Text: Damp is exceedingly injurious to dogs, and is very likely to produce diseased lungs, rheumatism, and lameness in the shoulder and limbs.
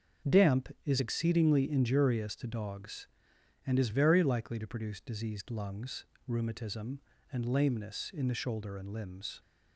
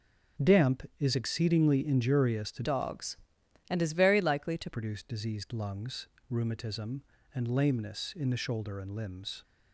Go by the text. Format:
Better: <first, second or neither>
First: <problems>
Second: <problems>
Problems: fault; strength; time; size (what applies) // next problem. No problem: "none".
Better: first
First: starts louder than the rest; until 1.4 s; 6 dB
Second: starts louder than the rest; until 1.5 s; 6.5 dB // changes voice from "dogs" to "to"; from 2.6 to 4.7 s; 2.1 s long